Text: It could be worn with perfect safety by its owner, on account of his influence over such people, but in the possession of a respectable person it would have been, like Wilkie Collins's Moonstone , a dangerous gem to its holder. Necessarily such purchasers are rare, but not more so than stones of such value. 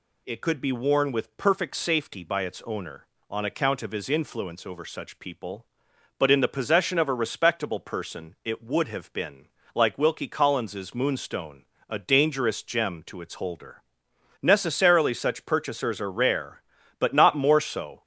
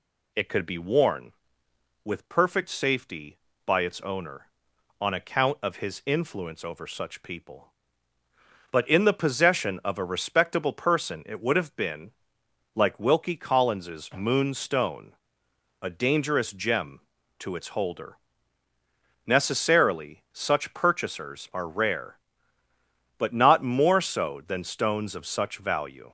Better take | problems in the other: second | stops before "than stones of such value"; at 18.0 s

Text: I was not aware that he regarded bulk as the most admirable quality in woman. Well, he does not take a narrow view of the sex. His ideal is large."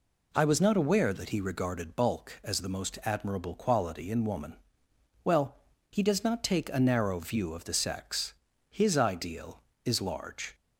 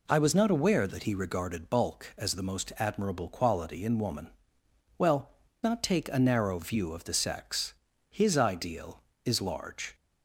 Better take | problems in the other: first | skips "he does"; at 5.4 s

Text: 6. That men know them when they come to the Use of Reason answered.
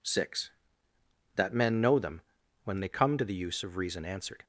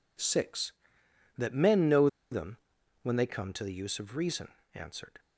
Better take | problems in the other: first | pauses between "know" and "them"; slight; at 2.0 s; 0.21 s long // pauses between "them" and "when"; noticeable; at 2.5 s; 0.46 s long; also in the first // pauses between "Reason" and "answered"; slight; at 4.4 s; 0.26 s long

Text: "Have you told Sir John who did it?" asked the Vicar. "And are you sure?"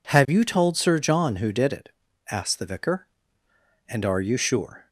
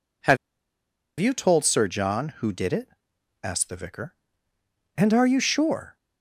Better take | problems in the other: first | pauses between "Have" and "you"; noticeable; at 0.3 s; 0.83 s long

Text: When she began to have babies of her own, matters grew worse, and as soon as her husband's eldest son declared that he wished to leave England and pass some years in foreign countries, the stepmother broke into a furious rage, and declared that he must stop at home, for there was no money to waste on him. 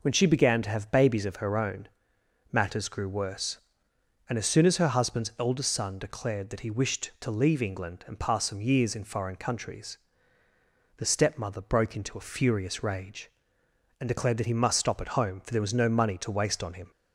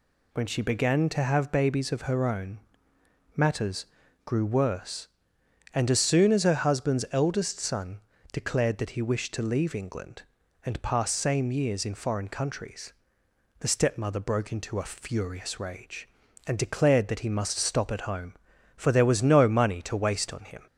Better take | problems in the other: first | pauses between "matters" and "grew"; at 3.8 s; 0.38 s long // pauses between "son" and "declared"; slight; at 7.9 s; 0.32 s long // says "same" for "some"; at 11.1 s

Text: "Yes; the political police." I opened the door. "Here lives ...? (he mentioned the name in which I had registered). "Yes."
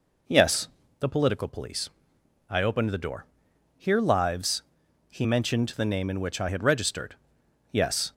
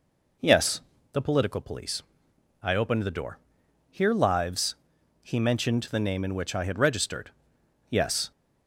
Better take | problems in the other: neither | none

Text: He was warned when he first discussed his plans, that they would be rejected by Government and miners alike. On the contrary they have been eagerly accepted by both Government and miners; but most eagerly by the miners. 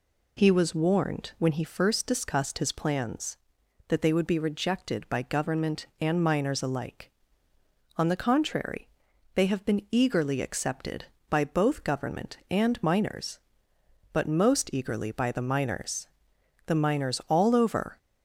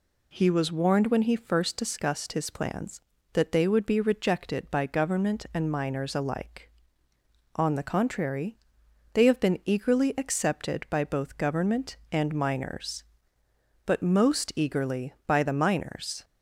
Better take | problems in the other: second | pauses between "contrary" and "they"; noticeable; at 8.8 s; 0.46 s long; noticeable in the second // goes on to say "The miners all over"; from 16.6 s on; 1.3 s long

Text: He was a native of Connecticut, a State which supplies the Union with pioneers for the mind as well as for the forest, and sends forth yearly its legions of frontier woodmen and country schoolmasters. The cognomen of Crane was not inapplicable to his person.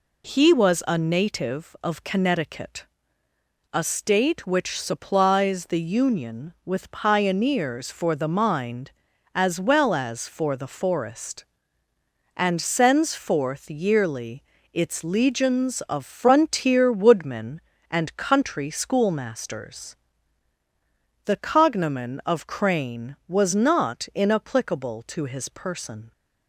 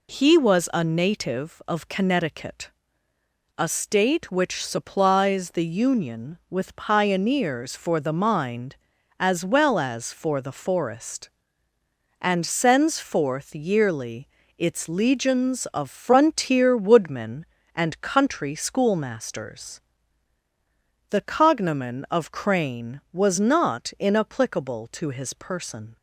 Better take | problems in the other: neither | pauses between "yearly" and "its"; slight; the same in both

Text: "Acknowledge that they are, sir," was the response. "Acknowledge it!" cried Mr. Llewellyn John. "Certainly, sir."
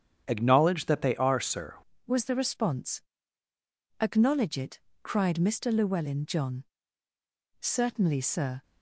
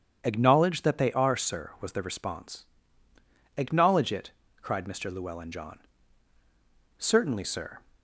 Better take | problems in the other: second | starts louder than the rest; strong; until 1.2 s; 8.5 dB; strong in the second // changes voice at "was"; from 2.0 s on; 6.6 s long

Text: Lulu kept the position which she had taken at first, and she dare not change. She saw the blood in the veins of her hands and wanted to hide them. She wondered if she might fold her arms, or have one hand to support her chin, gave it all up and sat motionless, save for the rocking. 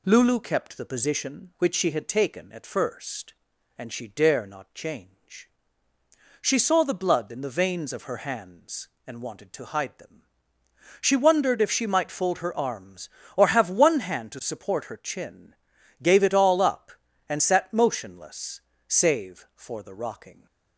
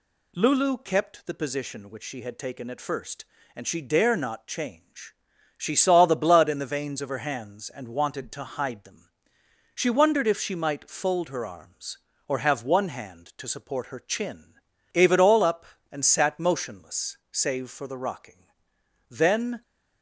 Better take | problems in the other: first | goes on to say "Then"; from 19.0 s on; 0.52 s long

